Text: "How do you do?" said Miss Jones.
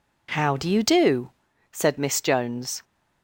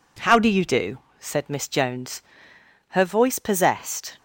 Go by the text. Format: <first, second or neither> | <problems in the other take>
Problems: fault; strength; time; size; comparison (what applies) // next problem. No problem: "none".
first | goes on to say "Her voice possessed"; noticeable; from 2.8 s on; 1.2 s long